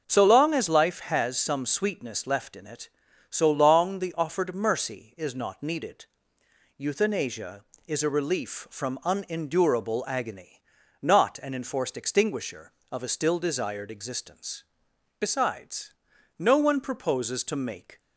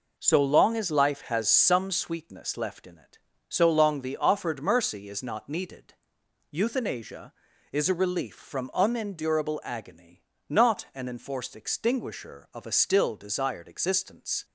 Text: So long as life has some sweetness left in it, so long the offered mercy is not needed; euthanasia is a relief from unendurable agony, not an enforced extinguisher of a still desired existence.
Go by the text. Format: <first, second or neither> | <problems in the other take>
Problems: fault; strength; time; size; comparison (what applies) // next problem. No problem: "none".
second | starts louder than the rest; until 1.0 s; 7 dB // goes on to say "Besides no one proposes to make"; strong; from 15.2 s on; 2.7 s long